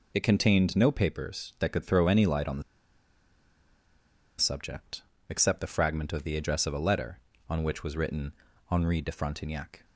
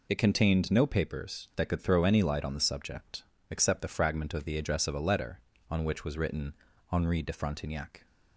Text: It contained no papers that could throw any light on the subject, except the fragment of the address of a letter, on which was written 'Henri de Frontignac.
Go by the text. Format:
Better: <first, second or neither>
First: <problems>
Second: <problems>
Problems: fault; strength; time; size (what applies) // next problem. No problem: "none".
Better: second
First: pauses between "the" and "subject"; strong; at 2.6 s; 1.7 s long // pauses between "written" and "Henri"; at 8.3 s; 0.38 s long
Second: pauses between "written" and "Henri"; at 6.5 s; 0.38 s long